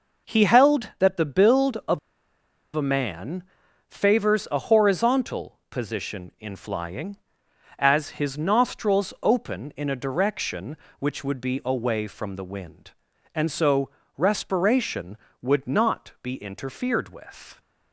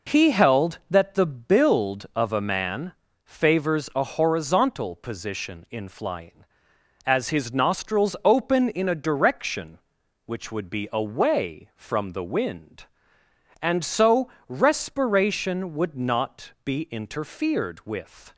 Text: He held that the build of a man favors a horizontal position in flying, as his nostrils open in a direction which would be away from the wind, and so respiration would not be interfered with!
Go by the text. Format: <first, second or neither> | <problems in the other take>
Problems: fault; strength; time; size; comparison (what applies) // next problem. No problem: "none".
second | pauses between "of" and "a"; noticeable; at 1.9 s; 0.76 s long // pauses between "man" and "favors"; noticeable; at 3.4 s; 0.46 s long; slight in the second // pauses between "so" and "respiration"; slight; at 13.8 s; 0.30 s long; slight in the second